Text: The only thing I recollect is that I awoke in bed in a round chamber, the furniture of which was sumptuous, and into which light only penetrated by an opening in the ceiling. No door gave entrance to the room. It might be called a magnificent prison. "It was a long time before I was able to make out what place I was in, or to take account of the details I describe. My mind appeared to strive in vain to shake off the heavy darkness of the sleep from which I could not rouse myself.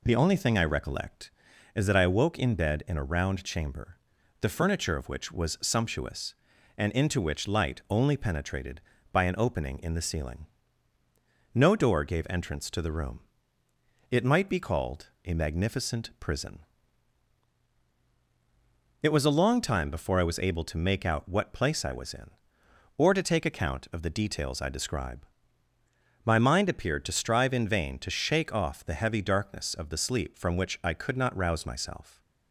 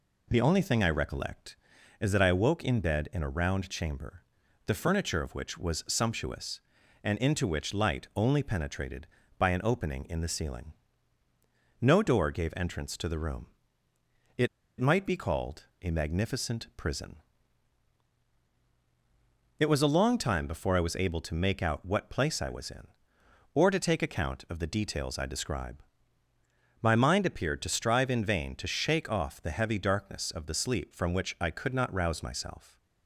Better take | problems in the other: first | pauses between "It" and "might"; slight; at 14.4 s; 0.33 s long

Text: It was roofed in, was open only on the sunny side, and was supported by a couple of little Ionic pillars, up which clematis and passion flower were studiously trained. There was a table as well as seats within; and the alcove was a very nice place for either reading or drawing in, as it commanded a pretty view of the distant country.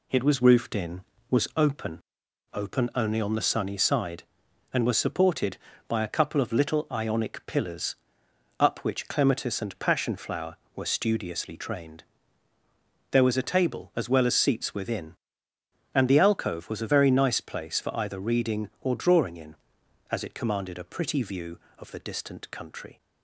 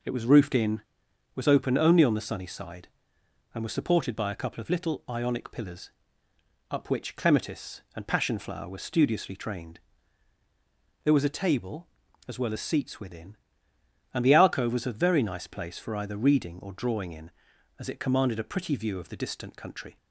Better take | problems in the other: second | says "open" twice; at 2.5 s

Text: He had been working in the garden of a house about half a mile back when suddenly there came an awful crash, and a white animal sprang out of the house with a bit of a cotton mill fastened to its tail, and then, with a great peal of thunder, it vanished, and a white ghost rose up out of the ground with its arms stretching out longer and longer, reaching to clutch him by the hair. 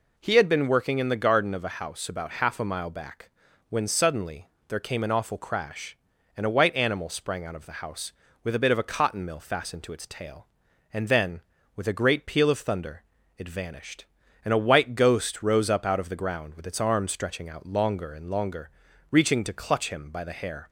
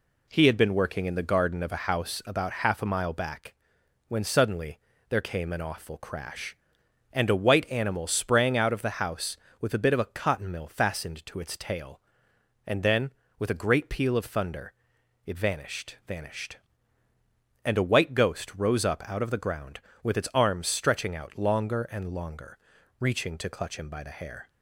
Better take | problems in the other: first | pauses between "back" and "when"; noticeable; at 3.5 s; 0.54 s long; also in the first // pauses between "suddenly" and "there"; slight; at 4.7 s; 0.30 s long; slight in the first // says "vanished" twice; at 16.0 s

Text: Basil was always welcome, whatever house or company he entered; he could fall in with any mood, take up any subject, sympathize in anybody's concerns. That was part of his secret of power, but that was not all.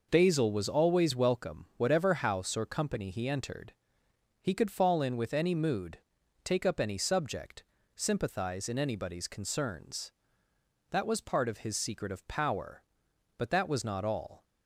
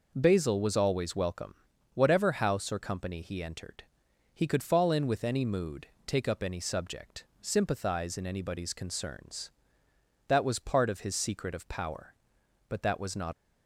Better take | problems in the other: first | stops before "all"; at 13.3 s

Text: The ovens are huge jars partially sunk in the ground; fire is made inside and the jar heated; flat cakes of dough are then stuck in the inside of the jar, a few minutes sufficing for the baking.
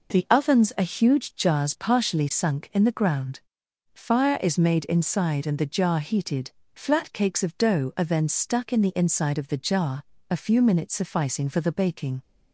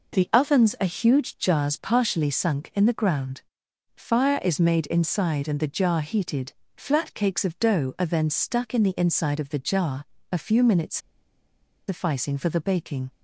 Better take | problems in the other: first | pauses between "minutes" and "sufficing"; noticeable; at 10.9 s; 0.90 s long

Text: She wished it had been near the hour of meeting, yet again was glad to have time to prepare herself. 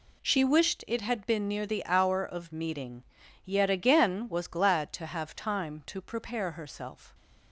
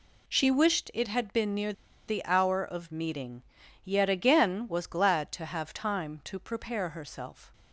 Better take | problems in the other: first | pauses between "near" and "the"; slight; at 1.7 s; 0.35 s long

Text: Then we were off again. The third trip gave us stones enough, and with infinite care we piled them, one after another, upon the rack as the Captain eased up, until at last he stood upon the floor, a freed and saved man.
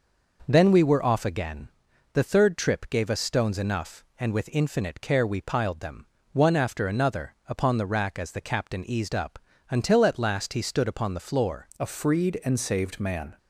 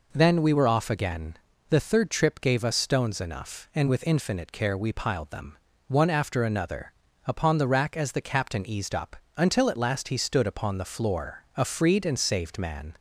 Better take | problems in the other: second | changes voice at "a"; from 11.7 s on; 1.6 s long

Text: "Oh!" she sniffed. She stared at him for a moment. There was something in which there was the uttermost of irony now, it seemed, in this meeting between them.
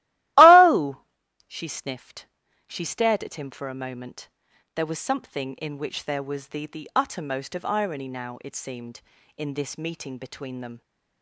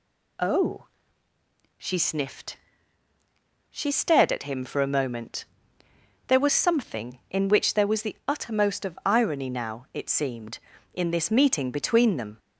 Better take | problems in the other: second | starts louder than the rest; strong; until 1.8 s; 16.5 dB // says "the" twice; at 6.6 s

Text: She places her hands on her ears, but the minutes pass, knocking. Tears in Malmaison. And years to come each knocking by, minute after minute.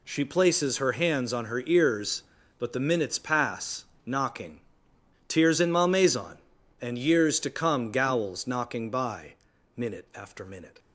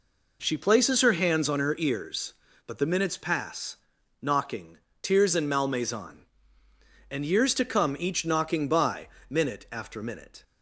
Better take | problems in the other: second | says "gowls" for "each"; at 7.9 s

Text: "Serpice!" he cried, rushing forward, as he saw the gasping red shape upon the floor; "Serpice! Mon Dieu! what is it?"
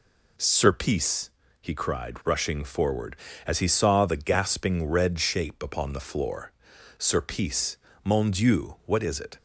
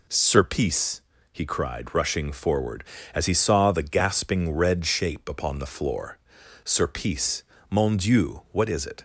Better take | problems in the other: neither | none

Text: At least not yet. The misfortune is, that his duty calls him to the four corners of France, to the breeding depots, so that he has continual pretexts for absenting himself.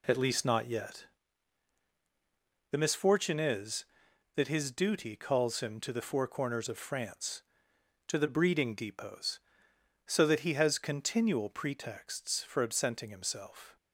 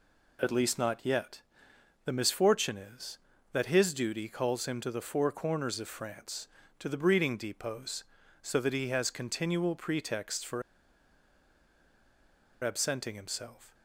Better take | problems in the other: first | pauses between "for" and "absenting"; strong; at 10.6 s; 2.0 s long

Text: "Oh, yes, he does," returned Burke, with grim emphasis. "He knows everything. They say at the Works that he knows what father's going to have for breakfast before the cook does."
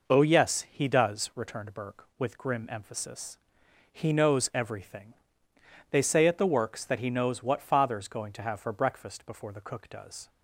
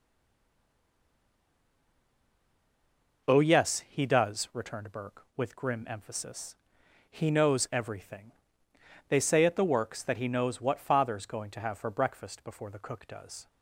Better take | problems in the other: first | stays silent before the first word; strong; until 3.2 s; 3.2 s long

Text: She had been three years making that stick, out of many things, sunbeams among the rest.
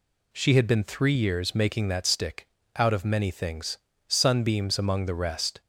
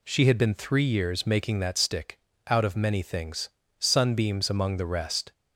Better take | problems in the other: neither | none

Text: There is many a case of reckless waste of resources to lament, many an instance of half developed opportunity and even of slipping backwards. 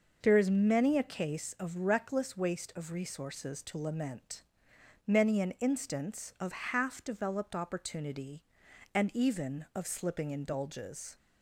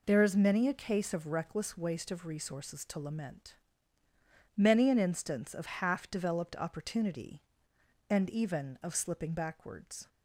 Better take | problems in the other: second | says "indulges" for "backwards"; at 10.3 s

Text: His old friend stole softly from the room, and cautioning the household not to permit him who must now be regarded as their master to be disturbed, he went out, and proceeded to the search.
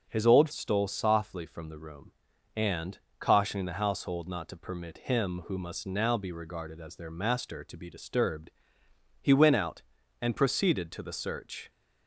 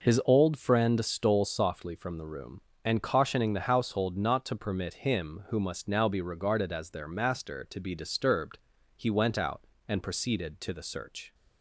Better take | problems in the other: second | starts louder than the rest; noticeable; until 1.1 s; 6 dB // skips "friend"; at 0.5 s // pauses between "and" and "cautioning"; slight; at 2.9 s; 0.20 s long

